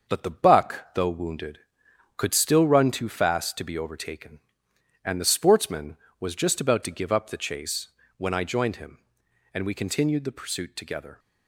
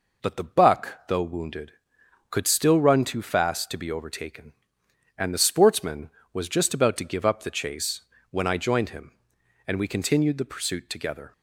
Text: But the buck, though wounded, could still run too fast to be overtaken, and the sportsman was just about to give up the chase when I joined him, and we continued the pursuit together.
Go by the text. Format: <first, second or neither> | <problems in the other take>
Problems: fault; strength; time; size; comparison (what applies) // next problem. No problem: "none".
second | gets quieter; noticeable; throughout; 4 dB // pauses between "chase" and "when"; slight; at 7.8 s; 0.28 s long; slight in the second